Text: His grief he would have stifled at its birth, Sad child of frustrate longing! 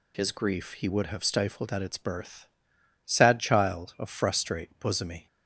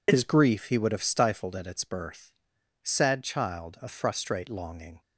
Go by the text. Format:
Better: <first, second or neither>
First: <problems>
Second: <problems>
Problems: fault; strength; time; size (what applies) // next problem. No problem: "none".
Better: second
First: says "bosomy" for "longing"; at 4.7 s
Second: none